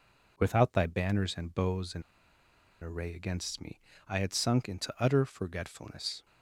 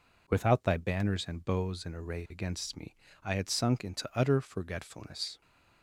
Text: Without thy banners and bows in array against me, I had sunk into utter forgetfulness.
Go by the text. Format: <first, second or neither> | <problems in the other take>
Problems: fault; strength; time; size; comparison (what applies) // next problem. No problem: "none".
second | pauses between "in" and "array"; noticeable; at 2.0 s; 0.80 s long